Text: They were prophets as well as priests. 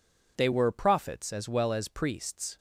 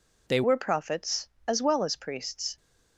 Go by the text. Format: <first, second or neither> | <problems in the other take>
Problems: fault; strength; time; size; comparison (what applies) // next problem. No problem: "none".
first | changes voice at "were"; from 0.4 s on; 2.1 s long